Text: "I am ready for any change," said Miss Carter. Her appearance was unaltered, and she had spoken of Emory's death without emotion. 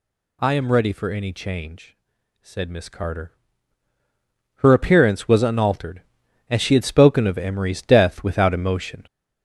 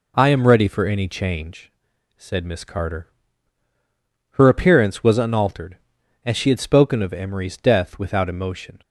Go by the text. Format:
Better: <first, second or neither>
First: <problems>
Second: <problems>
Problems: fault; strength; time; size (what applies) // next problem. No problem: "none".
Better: second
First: gets louder; noticeable; throughout; 5.5 dB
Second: none